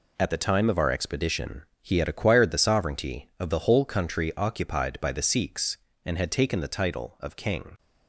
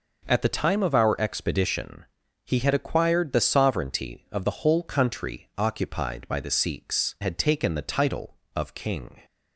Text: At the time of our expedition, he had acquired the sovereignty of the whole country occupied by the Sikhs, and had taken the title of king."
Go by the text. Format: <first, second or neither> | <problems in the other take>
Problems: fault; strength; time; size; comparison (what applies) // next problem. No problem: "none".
first | skips "and"; at 7.1 s